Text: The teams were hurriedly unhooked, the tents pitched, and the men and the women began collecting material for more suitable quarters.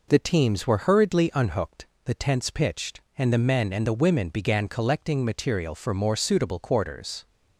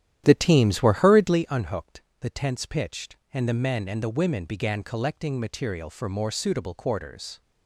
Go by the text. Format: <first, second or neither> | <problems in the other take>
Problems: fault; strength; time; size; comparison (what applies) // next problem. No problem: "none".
first | starts louder than the rest; strong; until 1.4 s; 11 dB